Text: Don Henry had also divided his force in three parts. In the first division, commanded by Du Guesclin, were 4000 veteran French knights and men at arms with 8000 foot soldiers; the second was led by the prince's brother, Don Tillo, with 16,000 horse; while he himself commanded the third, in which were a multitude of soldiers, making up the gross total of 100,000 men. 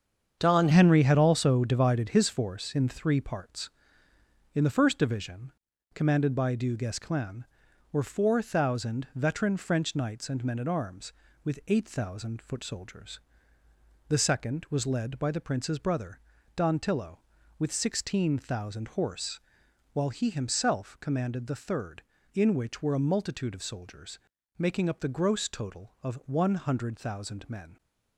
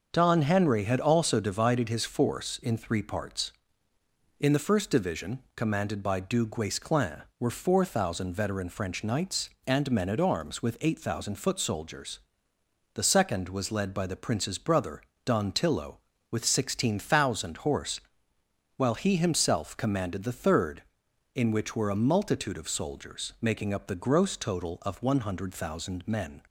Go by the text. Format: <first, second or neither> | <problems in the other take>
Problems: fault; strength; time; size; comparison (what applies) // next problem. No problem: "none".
second | starts louder than the rest; strong; until 1.4 s; 7.5 dB; noticeable in the second // changes voice at "Henry"; from 0.7 s on; 27.0 s long